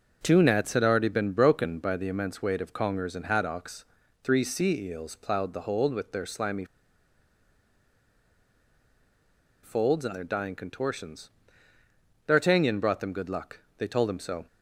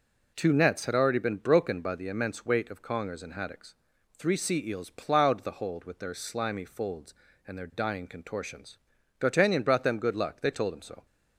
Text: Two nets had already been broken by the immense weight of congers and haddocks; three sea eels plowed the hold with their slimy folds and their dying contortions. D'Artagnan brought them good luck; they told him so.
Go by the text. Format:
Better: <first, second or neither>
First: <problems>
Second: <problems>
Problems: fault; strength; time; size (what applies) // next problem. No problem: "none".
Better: second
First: pauses between "slimy" and "folds"; strong; at 6.6 s; 2.9 s long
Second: none